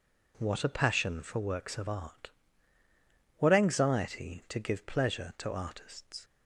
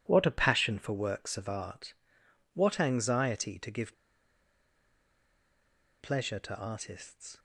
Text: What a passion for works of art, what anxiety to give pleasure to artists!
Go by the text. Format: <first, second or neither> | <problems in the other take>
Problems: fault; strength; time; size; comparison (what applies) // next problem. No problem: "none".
first | pauses between "give" and "pleasure"; strong; at 3.9 s; 2.0 s long